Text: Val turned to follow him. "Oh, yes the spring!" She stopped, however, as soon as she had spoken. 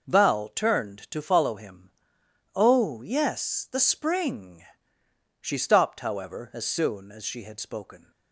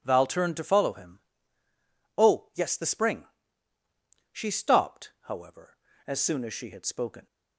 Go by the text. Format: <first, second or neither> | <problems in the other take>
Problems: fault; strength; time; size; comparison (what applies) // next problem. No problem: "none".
neither | none